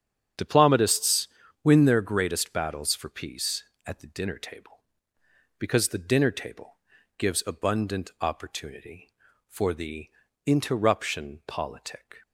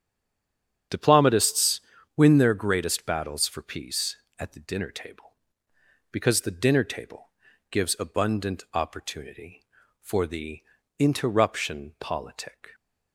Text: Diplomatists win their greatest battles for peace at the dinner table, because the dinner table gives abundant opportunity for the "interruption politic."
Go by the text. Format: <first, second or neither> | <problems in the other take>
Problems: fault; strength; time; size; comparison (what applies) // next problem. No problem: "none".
first | stays silent before the first word; slight; until 0.9 s; 0.9 s long // starts louder than the rest; strong; until 2.2 s; 8 dB; strong in the first // pauses between "Diplomatists" and "win"; slight; at 1.8 s; 0.34 s long; slight in the first // pauses between "table" and "gives"; at 7.2 s; 0.42 s long; also in the first // pauses between "the" and "interruption"; at 10.6 s; 0.38 s long; also in the first